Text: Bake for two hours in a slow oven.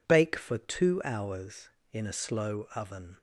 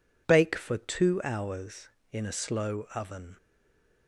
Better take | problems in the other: first | stays silent after the last word; slight; from 3.3 s on; 0.7 s long

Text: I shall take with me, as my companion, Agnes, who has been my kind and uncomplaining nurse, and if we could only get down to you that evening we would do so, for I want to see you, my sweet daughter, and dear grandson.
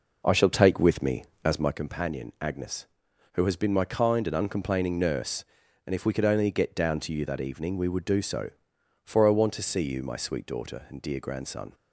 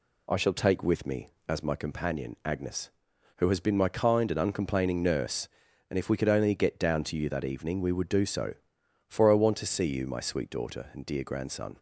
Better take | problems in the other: second | starts louder than the rest; noticeable; until 1.9 s; 5 dB

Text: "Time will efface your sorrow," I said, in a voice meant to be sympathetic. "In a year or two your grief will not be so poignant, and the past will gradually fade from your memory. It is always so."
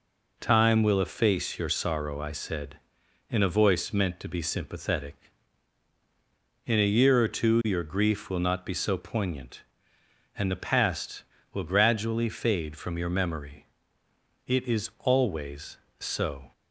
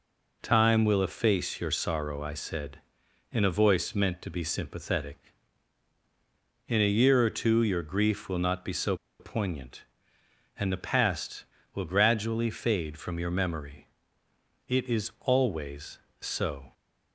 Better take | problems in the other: first | pauses between "so" and "poignant"; slight; at 8.9 s; 0.24 s long

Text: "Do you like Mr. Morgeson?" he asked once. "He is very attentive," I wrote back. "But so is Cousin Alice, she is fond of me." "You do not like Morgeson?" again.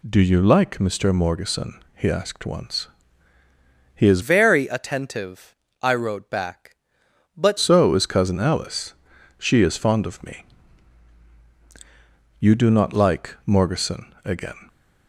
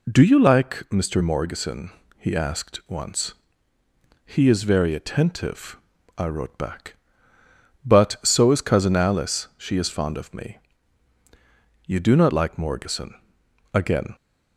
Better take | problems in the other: second | changes voice from "very" to "But"; from 4.2 to 7.5 s; 3.3 s long

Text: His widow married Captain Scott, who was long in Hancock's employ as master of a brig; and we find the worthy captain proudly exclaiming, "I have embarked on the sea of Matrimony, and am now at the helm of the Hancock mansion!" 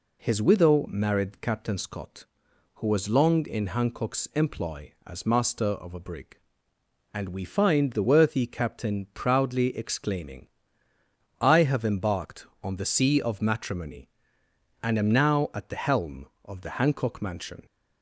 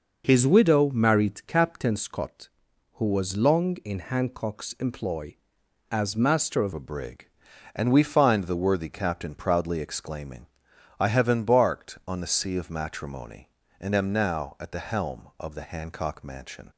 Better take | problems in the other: first | changes voice at "a"; from 6.7 s on; 10.0 s long

